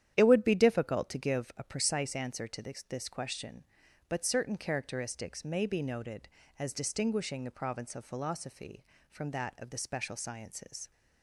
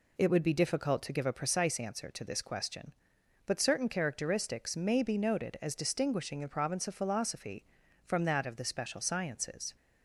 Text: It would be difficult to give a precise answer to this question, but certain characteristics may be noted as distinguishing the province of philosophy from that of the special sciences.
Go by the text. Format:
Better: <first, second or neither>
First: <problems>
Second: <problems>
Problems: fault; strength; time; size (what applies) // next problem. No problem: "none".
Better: second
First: starts louder than the rest; strong; until 1.1 s; 10.5 dB // says "this" twice; at 2.8 s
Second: none